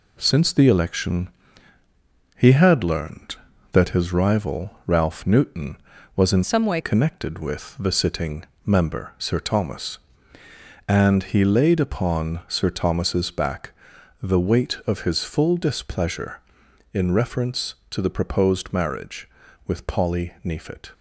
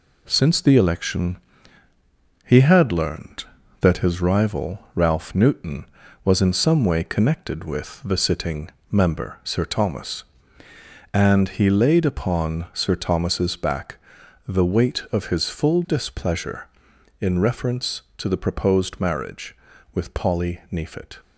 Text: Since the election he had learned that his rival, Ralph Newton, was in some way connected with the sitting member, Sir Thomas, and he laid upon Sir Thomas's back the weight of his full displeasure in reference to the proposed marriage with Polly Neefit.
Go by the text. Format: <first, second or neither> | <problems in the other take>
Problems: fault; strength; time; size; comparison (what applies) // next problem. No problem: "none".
second | pauses between "election" and "he"; at 1.2 s; 1.0 s long; also in the second // changes voice from "some" to "way"; from 6.4 to 6.8 s; 0.4 s long // pauses between "sitting" and "member"; slight; at 8.4 s; 0.22 s long; slight in the second // pauses between "back" and "the"; noticeable; at 13.7 s; 0.50 s long; noticeable in the second